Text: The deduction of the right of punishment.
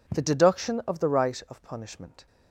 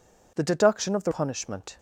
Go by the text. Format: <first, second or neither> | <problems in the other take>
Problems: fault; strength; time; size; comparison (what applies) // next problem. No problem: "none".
first | skips "right of"; at 1.1 s